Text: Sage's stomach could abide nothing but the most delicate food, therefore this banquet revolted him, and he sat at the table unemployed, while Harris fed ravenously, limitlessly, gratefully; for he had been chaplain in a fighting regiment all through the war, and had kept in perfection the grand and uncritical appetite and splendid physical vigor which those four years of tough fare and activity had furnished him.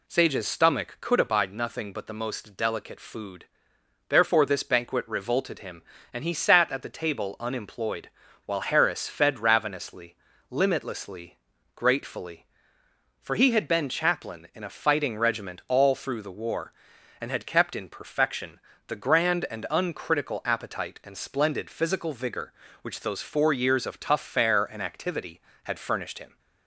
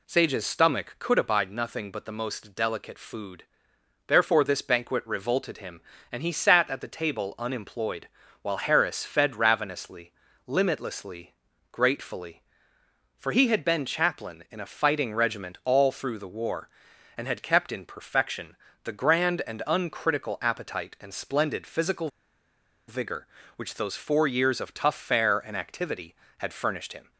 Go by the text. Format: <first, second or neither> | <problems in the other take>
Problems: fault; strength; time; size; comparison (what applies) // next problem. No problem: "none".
first | pauses between "perfection" and "the"; slight; at 18.5 s; 0.26 s long; slight in the first // pauses between "physical" and "vigor"; noticeable; at 22.1 s; 0.78 s long